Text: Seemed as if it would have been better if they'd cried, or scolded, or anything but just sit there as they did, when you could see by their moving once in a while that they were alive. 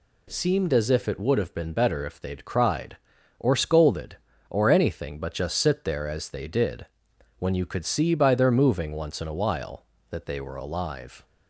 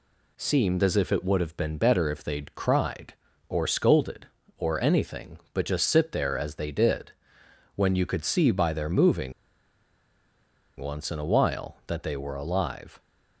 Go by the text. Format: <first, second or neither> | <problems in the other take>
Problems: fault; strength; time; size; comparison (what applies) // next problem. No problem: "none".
first | pauses between "moving" and "once"; strong; at 9.3 s; 1.4 s long